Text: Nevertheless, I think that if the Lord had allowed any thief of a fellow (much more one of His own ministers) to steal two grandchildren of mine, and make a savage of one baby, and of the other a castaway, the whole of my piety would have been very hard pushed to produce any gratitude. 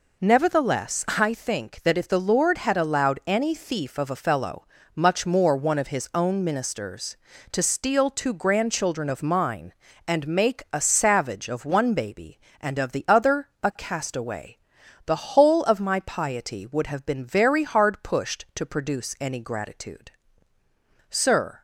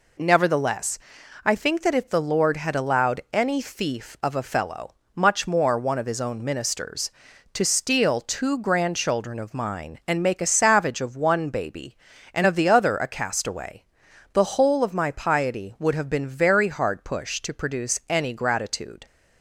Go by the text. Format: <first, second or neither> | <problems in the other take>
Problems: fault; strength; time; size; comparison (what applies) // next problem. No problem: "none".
second | goes on to say "Sir"; from 21.0 s on; 0.52 s long